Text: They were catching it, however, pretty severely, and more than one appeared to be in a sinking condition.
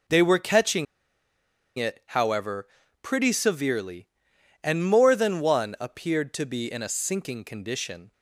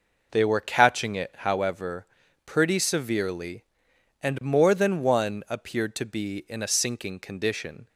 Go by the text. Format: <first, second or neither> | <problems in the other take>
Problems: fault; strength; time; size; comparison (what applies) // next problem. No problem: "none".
second | pauses between "catching" and "it"; noticeable; at 0.8 s; 0.92 s long